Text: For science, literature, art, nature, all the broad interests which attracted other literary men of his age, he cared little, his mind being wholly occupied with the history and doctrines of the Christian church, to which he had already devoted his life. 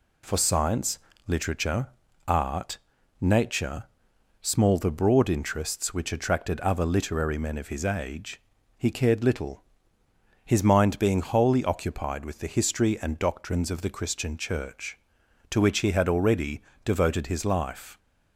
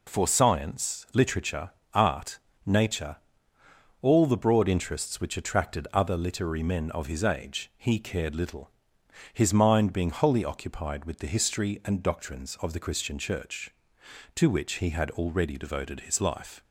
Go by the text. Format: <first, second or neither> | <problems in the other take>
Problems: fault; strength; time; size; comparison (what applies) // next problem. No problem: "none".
second | says "small" for "all"; at 4.4 s // pauses between "already" and "devoted"; slight; at 16.6 s; 0.22 s long